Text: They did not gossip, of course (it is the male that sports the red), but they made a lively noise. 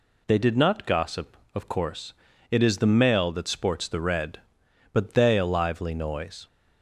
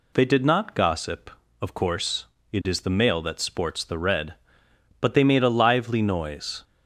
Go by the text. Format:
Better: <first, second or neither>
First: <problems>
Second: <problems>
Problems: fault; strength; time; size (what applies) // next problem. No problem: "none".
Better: second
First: skips "made"; at 5.3 s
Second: none